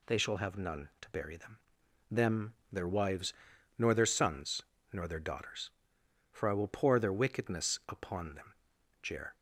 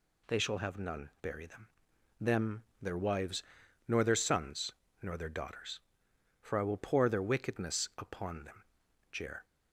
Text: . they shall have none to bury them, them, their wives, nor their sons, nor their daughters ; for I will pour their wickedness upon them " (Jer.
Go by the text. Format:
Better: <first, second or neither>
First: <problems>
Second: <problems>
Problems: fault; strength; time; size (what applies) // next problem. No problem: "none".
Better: first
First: none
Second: skips "to"; at 1.1 s